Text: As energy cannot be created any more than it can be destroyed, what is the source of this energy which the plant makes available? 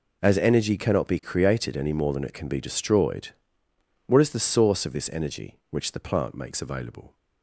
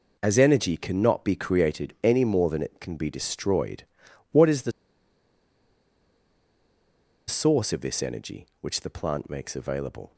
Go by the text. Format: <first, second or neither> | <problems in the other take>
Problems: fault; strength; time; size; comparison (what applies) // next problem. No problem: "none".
first | pauses between "the" and "source"; strong; at 4.7 s; 2.5 s long